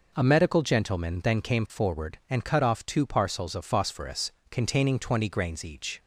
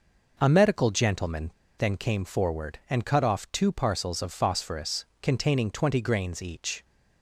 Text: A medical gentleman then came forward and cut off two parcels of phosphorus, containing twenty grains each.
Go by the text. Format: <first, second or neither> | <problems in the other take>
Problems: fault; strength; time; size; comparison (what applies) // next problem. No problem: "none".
first | pauses between "gentleman" and "then"; slight; at 1.4 s; 0.28 s long